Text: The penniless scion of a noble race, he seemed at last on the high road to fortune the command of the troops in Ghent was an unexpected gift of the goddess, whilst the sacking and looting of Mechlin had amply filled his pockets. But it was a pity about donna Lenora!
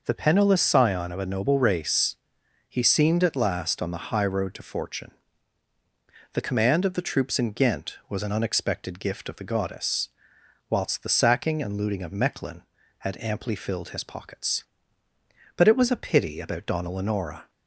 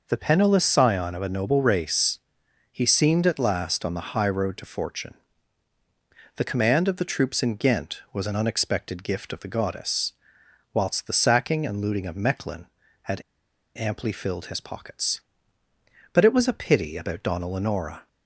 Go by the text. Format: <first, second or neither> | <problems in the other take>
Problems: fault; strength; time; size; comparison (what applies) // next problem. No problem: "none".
first | pauses between "fortune" and "the"; at 5.1 s; 1.2 s long; also in the first // pauses between "had" and "amply"; noticeable; at 13.2 s; 0.54 s long